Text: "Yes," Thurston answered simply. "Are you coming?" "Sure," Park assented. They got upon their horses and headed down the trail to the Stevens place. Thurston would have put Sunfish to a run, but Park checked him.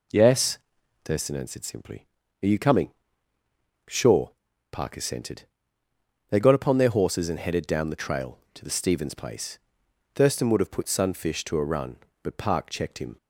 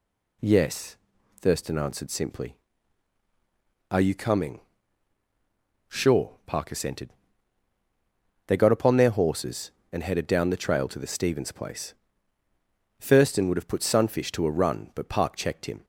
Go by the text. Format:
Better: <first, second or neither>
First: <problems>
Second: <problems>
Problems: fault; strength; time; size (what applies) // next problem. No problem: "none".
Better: second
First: starts louder than the rest; until 1.6 s; 3.5 dB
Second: none